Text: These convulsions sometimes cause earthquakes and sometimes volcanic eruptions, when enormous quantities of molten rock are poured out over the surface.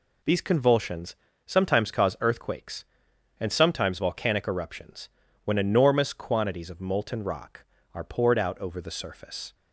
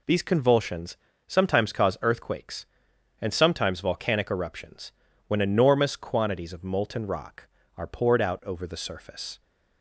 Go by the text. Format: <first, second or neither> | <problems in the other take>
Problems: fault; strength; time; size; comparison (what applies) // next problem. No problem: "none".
neither | pauses between "convulsions" and "sometimes"; slight; the same in both